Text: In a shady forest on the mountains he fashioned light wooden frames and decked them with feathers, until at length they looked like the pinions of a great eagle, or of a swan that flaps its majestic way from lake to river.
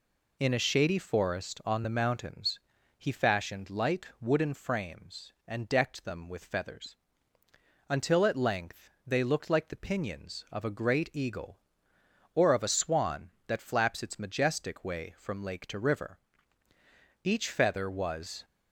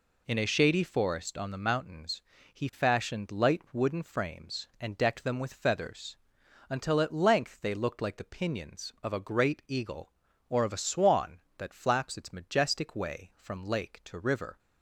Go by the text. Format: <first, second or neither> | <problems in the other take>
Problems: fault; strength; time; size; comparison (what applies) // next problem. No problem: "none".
second | pauses between "mountains" and "he"; at 2.5 s; 0.38 s long; slight in the second // pauses between "length" and "they"; slight; at 8.8 s; 0.18 s long // goes on to say "Each feather was"; noticeable; from 17.2 s on; 1.2 s long